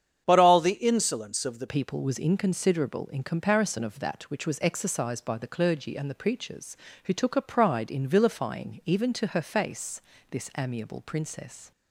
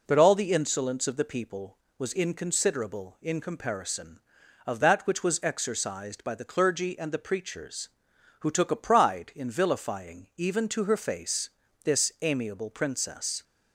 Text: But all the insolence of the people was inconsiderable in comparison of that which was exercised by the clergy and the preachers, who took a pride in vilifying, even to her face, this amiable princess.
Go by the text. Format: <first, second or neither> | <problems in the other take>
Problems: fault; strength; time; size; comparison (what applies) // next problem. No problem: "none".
second | starts louder than the rest; strong; until 1.2 s; 8.5 dB // changes voice at "people"; from 1.6 s on; 10.1 s long